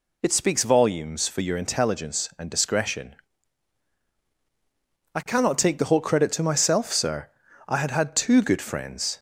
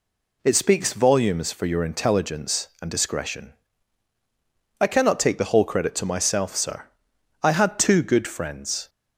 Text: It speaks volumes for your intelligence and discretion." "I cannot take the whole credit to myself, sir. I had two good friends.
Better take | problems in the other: second | says "had" twice; at 7.9 s

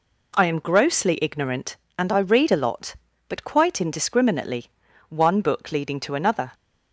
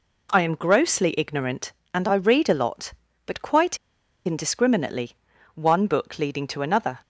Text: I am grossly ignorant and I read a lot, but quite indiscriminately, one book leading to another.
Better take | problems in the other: first | pauses between "quite" and "indiscriminately"; noticeable; at 3.7 s; 0.50 s long

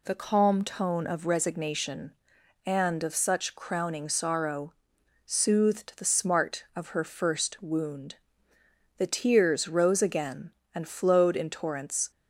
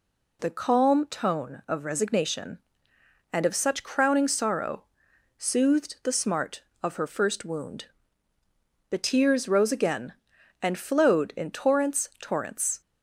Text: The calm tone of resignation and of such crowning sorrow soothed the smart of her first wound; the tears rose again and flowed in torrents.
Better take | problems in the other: first | pauses between "sorrow" and "soothed"; noticeable; at 4.8 s; 0.52 s long; noticeable in the first // says "torrents" twice; at 12.2 s

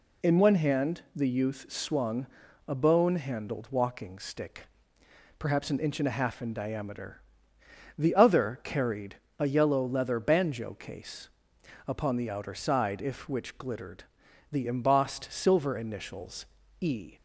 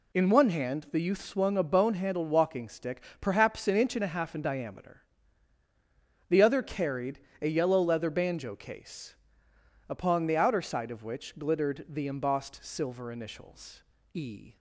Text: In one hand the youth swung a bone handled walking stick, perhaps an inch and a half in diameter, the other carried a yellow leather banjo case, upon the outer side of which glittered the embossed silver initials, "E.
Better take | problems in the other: second | pauses between "swung" and "a"; at 2.2 s; 0.40 s long // pauses between "carried" and "a"; slight; at 9.1 s; 0.24 s long; slight in the second // says "if" for "of"; at 13.0 s // pauses between "glittered" and "the"; noticeable; at 14.0 s; 0.48 s long

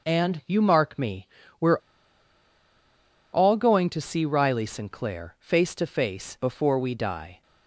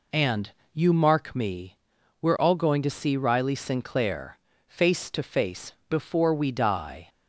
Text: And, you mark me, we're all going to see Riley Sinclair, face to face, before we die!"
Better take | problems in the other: second | pauses between "we're" and "all"; strong; at 1.7 s; 1.5 s long

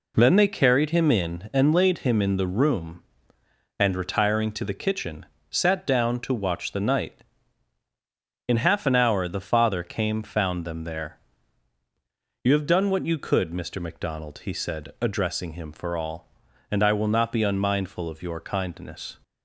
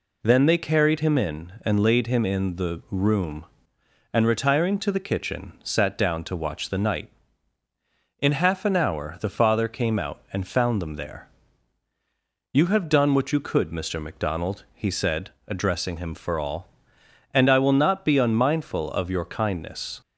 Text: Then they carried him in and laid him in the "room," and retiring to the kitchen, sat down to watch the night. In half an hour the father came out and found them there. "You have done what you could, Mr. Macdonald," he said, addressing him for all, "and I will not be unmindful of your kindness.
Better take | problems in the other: second | skips "out and"; at 10.2 s

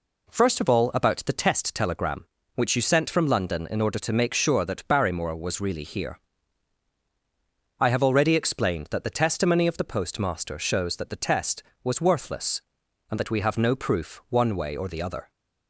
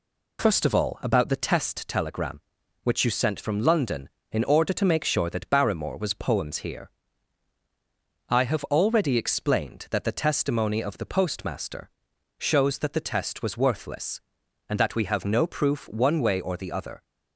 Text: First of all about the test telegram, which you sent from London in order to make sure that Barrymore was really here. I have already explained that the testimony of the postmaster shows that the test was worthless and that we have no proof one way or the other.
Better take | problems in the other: first | says "poems" for "really"; at 6.1 s // pauses between "postmaster" and "shows"; noticeable; at 11.9 s; 0.48 s long

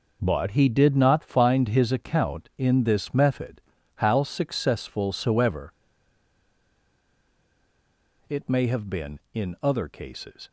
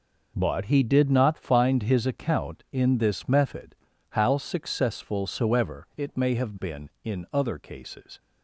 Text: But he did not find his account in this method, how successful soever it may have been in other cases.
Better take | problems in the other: second | pauses between "soever" and "it"; strong; at 5.7 s; 2.5 s long

